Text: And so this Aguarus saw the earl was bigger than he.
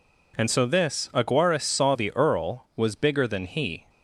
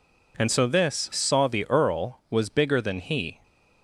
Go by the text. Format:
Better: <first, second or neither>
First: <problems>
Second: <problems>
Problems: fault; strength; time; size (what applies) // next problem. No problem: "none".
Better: first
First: none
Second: skips "Aguarus"; at 1.1 s